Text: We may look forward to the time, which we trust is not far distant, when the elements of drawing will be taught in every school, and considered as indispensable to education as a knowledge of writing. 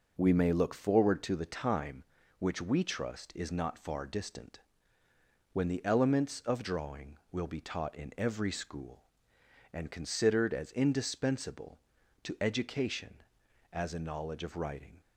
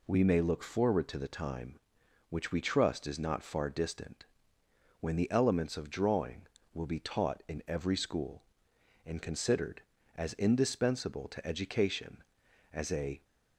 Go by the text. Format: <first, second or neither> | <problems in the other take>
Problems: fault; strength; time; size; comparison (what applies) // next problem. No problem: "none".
first | stops before "knowledge of writing"; at 13.2 s